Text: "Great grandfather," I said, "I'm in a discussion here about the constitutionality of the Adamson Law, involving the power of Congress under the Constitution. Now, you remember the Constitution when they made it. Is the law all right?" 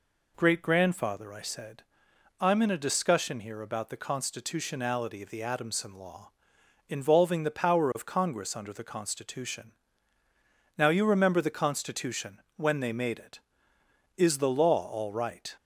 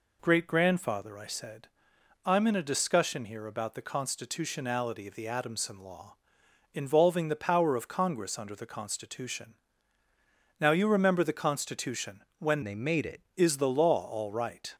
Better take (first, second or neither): first